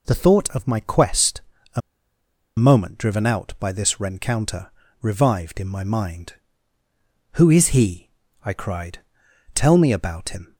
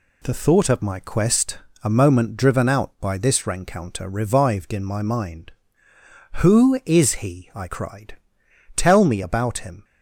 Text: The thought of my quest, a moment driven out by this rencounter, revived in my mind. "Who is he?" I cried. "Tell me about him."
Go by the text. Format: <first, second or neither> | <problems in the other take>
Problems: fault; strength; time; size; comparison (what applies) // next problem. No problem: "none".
second | pauses between "a" and "moment"; noticeable; at 1.8 s; 0.76 s long